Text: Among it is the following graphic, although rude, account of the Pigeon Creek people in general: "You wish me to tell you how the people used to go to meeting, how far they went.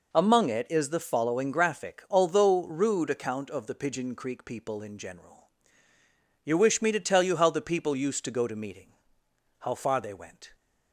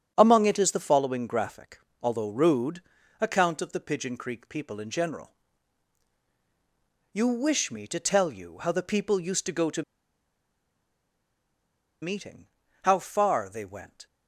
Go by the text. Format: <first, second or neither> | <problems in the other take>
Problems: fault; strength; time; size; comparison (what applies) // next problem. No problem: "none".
first | starts louder than the rest; strong; until 1.1 s; 8 dB // pauses between "to" and "meeting"; strong; at 9.8 s; 2.2 s long